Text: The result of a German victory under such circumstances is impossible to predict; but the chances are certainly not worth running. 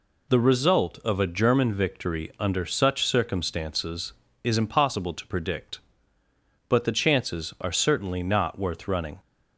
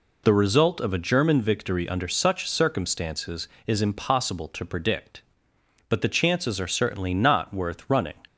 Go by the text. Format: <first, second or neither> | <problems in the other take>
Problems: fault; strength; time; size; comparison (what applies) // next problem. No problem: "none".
neither | none